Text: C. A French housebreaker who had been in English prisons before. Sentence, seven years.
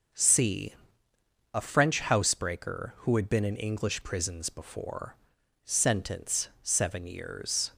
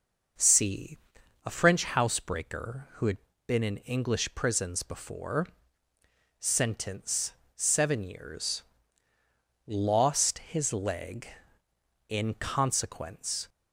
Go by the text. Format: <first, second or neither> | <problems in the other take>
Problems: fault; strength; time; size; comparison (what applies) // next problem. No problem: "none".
first | pauses between "had" and "been"; slight; at 3.1 s; 0.30 s long // goes on to say "Lost his leg in consequence"; strong; from 9.6 s on; 3.8 s long